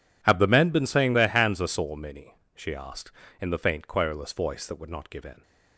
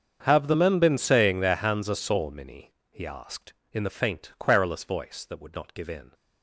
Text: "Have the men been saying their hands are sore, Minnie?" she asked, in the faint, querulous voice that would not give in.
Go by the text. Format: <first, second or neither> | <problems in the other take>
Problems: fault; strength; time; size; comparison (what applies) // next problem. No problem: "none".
first | starts louder than the rest; strong; until 1.2 s; 7 dB // says "he" for "she"; at 2.8 s